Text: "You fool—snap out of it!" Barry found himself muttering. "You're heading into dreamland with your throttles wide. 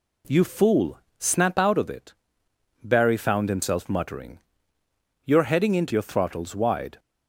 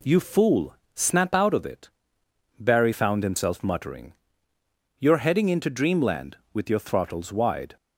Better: second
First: skips "dreamland with"; at 5.9 s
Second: none

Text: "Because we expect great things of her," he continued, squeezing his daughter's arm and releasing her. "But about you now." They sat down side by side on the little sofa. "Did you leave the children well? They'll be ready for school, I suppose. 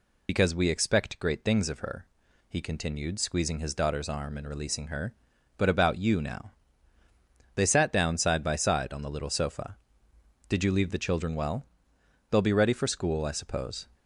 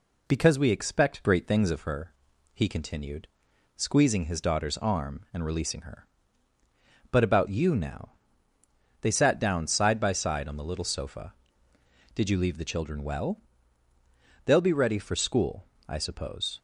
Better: second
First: loses the start of "Because"; at 0.2 s; 120 ms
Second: none

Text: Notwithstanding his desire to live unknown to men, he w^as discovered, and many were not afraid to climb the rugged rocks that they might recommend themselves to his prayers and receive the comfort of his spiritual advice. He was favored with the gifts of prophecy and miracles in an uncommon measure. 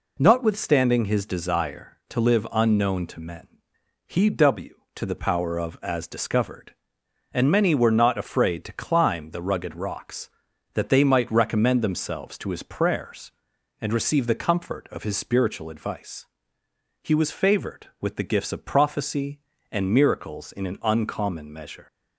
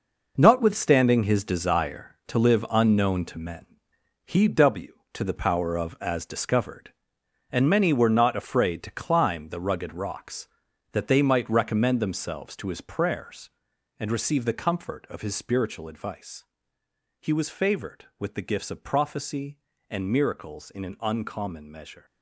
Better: first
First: none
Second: gets quieter; strong; throughout; 10.5 dB

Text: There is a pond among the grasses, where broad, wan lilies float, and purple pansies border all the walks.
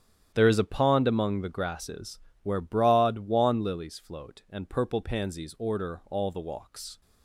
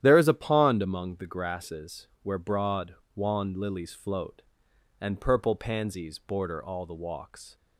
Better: second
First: starts louder than the rest; strong; until 1.3 s; 10 dB // says "order" for "border"; at 5.5 s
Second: starts louder than the rest; strong; until 1.0 s; 11 dB

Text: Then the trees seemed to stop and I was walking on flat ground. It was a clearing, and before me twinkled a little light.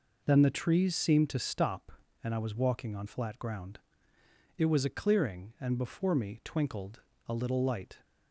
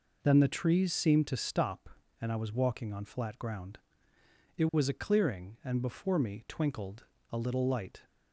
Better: neither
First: pauses between "twinkled" and "a"; slight; at 7.0 s; 0.26 s long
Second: pauses between "twinkled" and "a"; slight; at 7.0 s; 0.26 s long

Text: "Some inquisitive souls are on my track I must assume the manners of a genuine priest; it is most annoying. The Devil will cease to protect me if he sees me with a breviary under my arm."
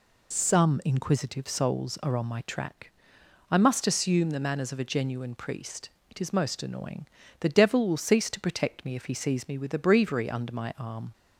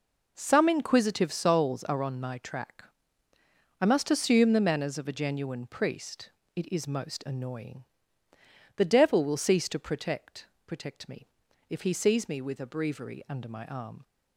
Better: first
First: pauses between "track" and "I"; noticeable; at 2.8 s; 0.60 s long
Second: pauses between "track" and "I"; noticeable; at 2.8 s; 0.96 s long // says "protect" twice; at 10.6 s // pauses between "me" and "if"; at 11.2 s; 0.44 s long

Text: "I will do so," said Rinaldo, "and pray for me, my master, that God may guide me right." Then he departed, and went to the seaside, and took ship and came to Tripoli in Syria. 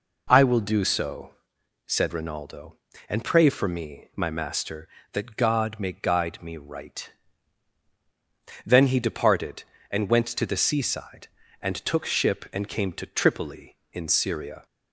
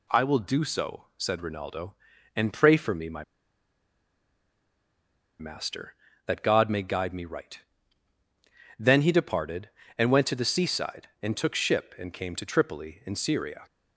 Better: first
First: none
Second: pauses between "my" and "master"; strong; at 3.2 s; 2.1 s long

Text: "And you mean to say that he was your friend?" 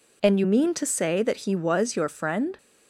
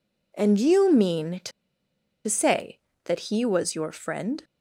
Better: first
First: none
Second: pauses between "to" and "say"; noticeable; at 1.5 s; 0.76 s long

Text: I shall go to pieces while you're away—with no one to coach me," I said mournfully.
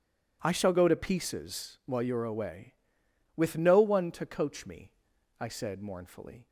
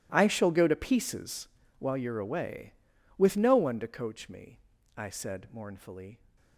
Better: first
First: none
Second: gets quieter; strong; throughout; 18 dB // pauses between "pieces" and "while"; slight; at 1.4 s; 0.32 s long

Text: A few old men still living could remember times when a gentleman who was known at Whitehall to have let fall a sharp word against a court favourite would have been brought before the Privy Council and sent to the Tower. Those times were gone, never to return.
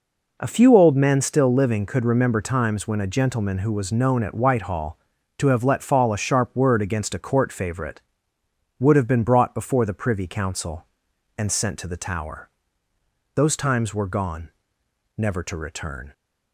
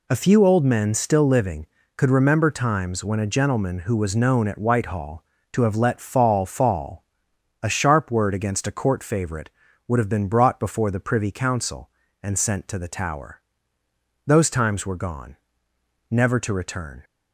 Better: first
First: none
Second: says "fall" twice; at 6.4 s

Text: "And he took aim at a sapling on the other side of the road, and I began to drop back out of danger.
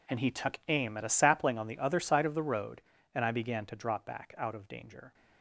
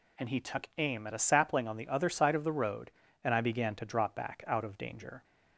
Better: second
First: gets quieter; strong; throughout; 15.5 dB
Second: none

